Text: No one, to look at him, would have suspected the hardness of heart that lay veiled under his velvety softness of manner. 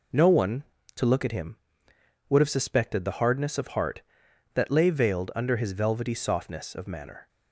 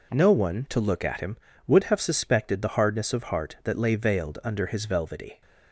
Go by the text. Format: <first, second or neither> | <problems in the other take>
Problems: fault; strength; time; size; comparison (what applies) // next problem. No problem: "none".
first | stops before "softness of manner"; at 5.4 s